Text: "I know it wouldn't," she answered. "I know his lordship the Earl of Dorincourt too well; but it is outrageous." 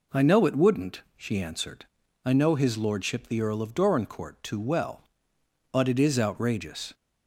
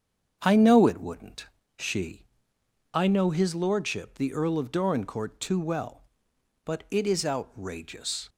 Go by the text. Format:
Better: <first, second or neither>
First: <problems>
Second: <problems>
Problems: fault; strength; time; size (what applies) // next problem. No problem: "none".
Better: first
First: none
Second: starts louder than the rest; strong; until 1.4 s; 7.5 dB // skips "answered"; at 2.5 s